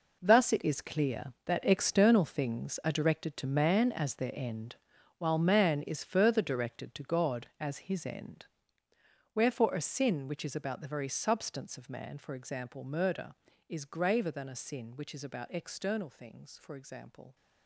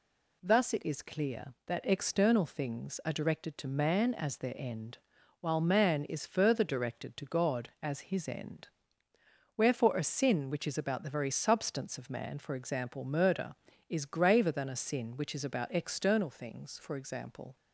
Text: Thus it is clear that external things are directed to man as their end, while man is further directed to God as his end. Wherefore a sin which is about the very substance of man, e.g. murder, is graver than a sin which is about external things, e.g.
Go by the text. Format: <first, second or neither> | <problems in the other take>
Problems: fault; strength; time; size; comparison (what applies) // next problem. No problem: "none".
second | gets quieter; strong; throughout; 12.5 dB